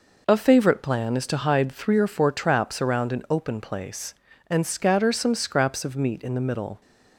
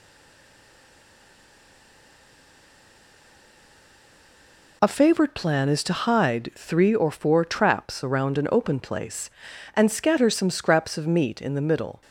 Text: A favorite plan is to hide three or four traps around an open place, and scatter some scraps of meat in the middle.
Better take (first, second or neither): first